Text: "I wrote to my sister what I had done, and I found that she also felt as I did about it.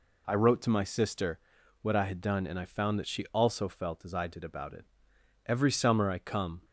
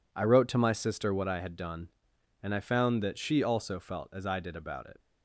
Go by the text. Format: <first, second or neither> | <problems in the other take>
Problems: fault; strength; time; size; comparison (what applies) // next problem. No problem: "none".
second | pauses between "sister" and "what"; at 1.3 s; 0.42 s long // goes on to say "Every summer I come"; noticeable; from 5.4 s on; 1.2 s long